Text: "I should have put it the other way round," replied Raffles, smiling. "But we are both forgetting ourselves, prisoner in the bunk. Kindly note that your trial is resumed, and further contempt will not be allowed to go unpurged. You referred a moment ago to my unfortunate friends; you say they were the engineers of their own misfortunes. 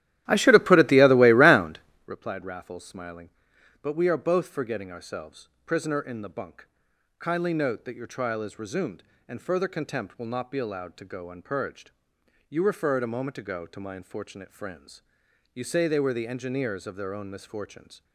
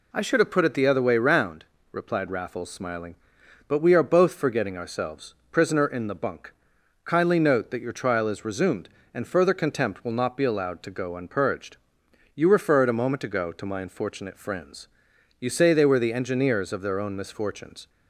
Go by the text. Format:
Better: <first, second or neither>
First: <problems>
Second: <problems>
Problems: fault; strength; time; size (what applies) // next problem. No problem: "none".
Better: second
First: starts louder than the rest; strong; until 2.2 s; 13.5 dB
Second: none